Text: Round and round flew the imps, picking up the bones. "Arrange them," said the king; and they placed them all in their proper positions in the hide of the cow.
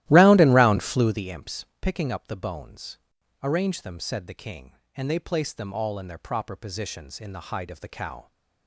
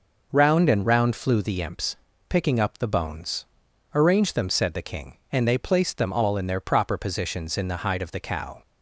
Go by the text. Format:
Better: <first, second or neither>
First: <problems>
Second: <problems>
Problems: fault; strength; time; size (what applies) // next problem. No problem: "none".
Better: second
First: starts louder than the rest; strong; until 1.3 s; 15 dB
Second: none